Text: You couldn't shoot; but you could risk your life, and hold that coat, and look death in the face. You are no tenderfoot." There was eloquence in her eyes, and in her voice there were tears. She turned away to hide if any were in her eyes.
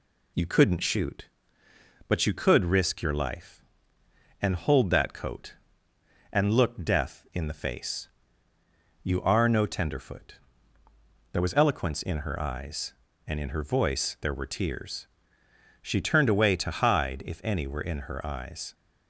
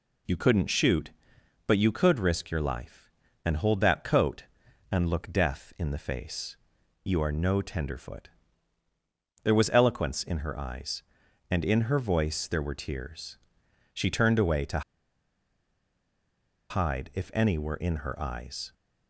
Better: first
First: none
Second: pauses between "to" and "hide"; strong; at 14.8 s; 1.8 s long

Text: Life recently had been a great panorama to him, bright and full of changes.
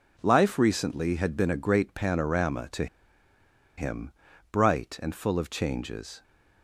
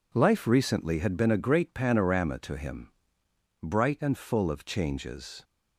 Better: second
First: pauses between "to" and "him"; noticeable; at 2.8 s; 0.93 s long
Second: none

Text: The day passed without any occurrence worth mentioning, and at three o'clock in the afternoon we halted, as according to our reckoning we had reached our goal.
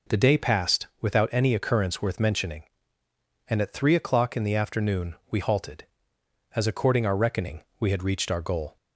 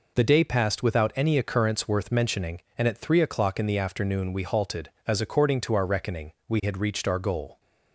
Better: second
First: skips "to"; at 7.0 s // pauses between "reckoning" and "we"; slight; at 7.6 s; 0.16 s long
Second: none

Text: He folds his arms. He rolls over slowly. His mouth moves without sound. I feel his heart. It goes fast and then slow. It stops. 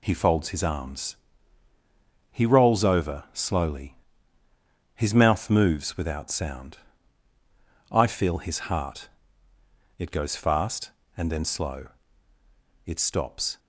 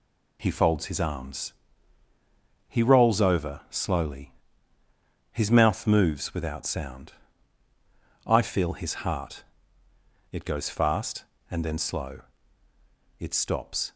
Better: neither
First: none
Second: none

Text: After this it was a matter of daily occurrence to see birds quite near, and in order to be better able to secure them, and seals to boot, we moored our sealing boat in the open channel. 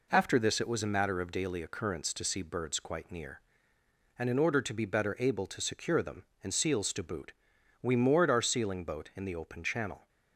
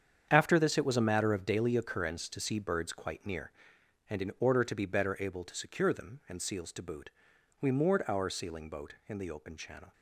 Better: first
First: none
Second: gets quieter; strong; throughout; 11.5 dB

